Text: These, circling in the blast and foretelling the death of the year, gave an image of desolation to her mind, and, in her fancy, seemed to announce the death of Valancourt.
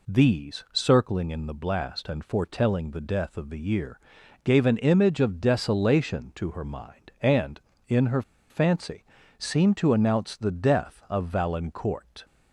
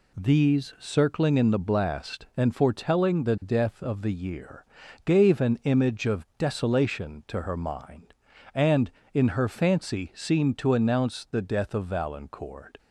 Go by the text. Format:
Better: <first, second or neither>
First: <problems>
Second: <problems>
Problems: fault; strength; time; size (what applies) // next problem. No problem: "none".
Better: second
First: pauses between "her" and "fancy"; slight; at 8.2 s; 0.29 s long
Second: none